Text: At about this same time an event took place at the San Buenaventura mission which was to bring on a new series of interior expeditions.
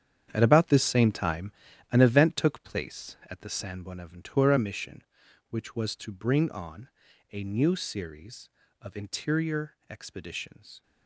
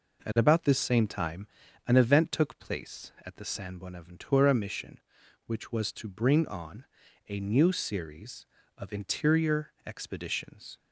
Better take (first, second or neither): second